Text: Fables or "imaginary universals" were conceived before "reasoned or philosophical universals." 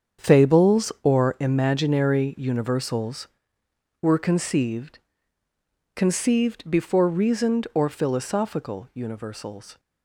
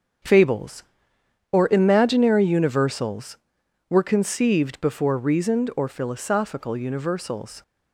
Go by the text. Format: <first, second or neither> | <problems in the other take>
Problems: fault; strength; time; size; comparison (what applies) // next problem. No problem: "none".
second | starts louder than the rest; strong; until 1.3 s; 7.5 dB; strong in the second // says "conceived" twice; at 5.9 s